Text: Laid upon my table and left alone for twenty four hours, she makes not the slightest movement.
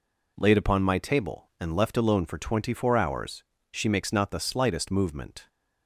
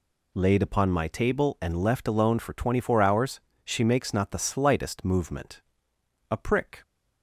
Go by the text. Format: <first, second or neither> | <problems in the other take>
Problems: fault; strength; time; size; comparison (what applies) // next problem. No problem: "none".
first | goes on to say "A prick"; from 6.3 s on; 0.52 s long